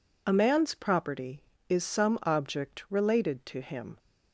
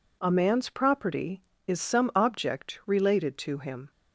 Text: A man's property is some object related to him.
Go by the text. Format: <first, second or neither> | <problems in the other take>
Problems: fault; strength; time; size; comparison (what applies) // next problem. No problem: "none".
neither | none